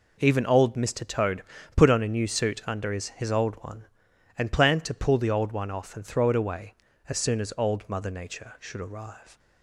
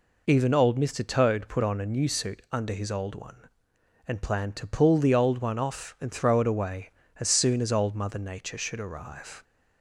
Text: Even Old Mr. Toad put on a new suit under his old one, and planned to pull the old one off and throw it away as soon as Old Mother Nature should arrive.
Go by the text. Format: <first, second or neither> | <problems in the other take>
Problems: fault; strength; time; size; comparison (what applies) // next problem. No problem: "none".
second | pauses between "Toad" and "put"; slight; at 1.4 s; 0.32 s long // says "his" twice; at 3.0 s